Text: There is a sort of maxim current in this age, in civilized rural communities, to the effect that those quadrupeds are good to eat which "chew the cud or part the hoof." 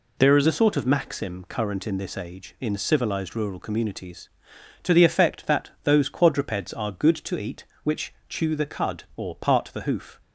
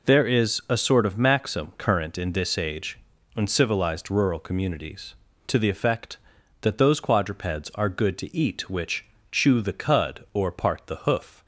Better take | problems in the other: second | changes voice at "a"; from 0.4 s on; 9.8 s long // pauses between "which" and "chew"; slight; at 8.1 s; 0.16 s long; slight in the second

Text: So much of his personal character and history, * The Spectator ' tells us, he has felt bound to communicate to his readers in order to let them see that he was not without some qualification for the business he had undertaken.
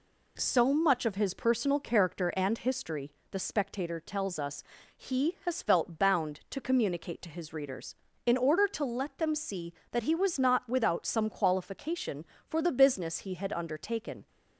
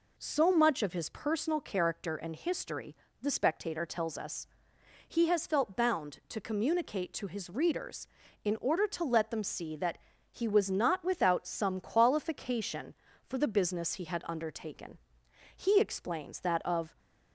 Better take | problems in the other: first | pauses between "that" and "he"; slight; at 9.9 s; 0.34 s long // goes on to say "He explains that of"; from 15.6 s on; 1.3 s long

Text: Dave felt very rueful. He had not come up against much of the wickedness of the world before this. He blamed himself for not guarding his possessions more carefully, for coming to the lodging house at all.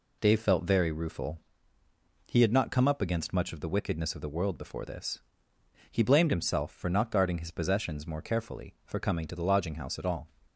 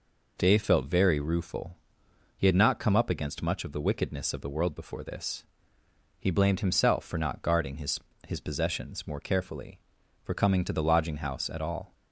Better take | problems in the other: first | says "his" twice; at 8.2 s

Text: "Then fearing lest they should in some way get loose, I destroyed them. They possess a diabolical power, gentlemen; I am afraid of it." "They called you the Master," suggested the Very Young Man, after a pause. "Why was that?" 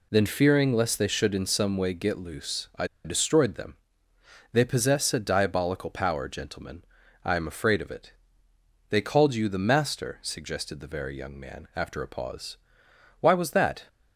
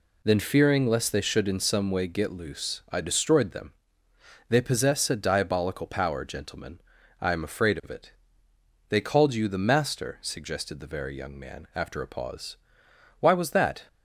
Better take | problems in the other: second | pauses between "I" and "destroyed"; slight; at 2.8 s; 0.18 s long

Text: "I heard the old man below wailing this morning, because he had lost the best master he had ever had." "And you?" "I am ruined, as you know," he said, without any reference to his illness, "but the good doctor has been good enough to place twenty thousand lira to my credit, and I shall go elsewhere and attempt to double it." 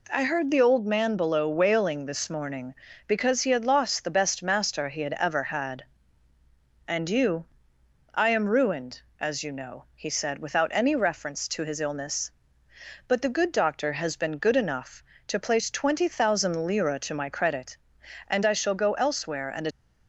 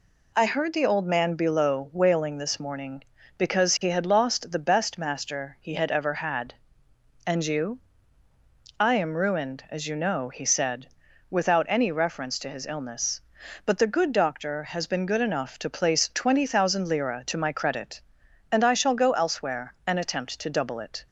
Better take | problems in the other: second | stops before "attempt to double it"; at 19.7 s

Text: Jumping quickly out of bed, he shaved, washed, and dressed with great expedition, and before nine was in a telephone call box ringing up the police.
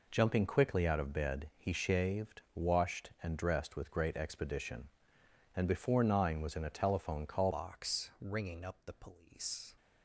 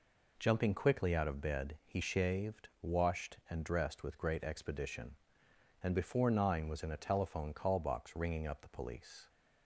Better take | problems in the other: second | changes voice at "box"; from 7.5 s on; 2.1 s long

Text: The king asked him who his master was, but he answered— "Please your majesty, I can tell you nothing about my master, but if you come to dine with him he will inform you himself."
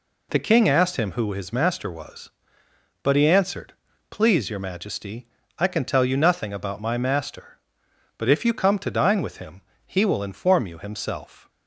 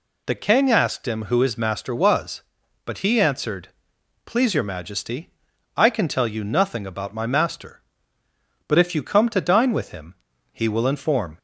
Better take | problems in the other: first | pauses between "him" and "he"; at 10.1 s; 0.38 s long; slight in the first // stops before "you himself"; at 11.3 s

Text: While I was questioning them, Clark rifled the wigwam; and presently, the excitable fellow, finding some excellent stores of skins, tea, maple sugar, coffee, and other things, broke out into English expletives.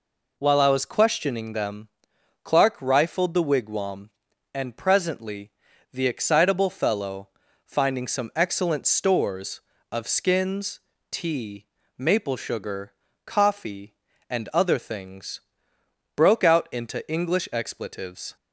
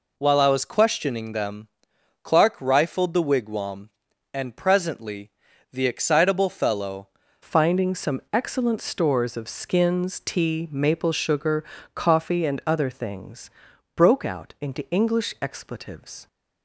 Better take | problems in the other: first | changes voice at "finding"; from 7.4 s on; 8.8 s long

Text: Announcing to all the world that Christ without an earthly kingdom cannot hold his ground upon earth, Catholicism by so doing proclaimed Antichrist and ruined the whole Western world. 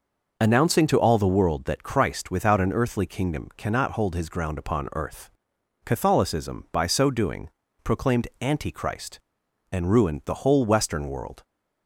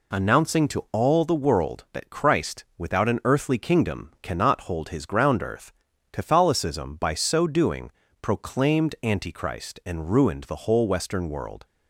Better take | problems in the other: first | skips "upon"; at 5.4 s // pauses between "doing" and "proclaimed"; slight; at 7.9 s; 0.30 s long; slight in the first

